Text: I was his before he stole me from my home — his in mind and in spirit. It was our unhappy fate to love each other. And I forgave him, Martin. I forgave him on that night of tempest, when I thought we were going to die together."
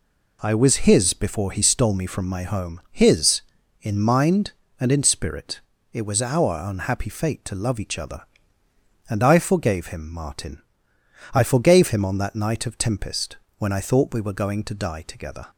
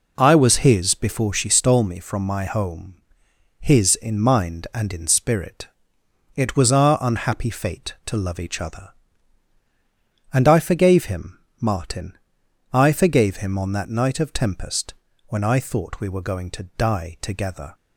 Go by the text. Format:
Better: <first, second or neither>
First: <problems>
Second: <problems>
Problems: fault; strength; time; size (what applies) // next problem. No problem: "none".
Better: first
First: none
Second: says "she" for "he"; at 1.3 s